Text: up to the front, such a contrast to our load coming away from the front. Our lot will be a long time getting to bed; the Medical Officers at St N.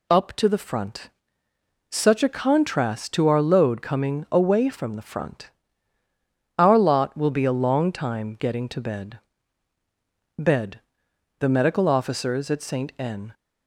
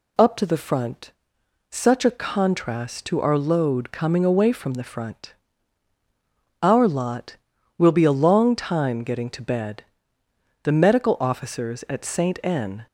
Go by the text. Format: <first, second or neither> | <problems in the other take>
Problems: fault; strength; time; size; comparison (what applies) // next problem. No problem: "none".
second | says "bed" twice; at 10.3 s